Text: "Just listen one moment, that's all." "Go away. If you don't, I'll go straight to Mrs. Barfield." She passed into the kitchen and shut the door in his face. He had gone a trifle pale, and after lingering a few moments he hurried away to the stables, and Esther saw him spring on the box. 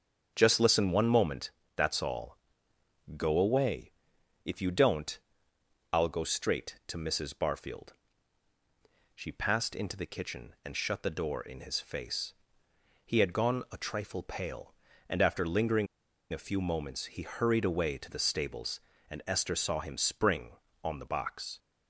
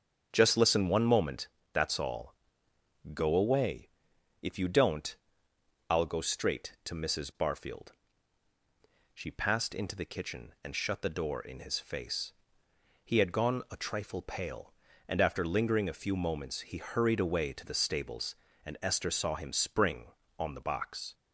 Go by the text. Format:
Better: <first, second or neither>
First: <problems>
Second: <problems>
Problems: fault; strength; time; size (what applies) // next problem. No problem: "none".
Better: second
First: starts louder than the rest; strong; until 1.3 s; 7.5 dB // pauses between "lingering" and "a"; at 15.8 s; 0.45 s long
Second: starts louder than the rest; strong; until 1.3 s; 7.5 dB